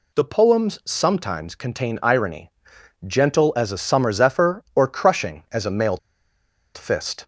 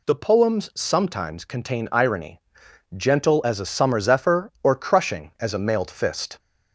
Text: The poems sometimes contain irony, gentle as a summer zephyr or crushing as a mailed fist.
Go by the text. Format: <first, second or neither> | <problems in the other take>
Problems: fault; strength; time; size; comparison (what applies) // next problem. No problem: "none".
second | pauses between "mailed" and "fist"; noticeable; at 5.9 s; 0.78 s long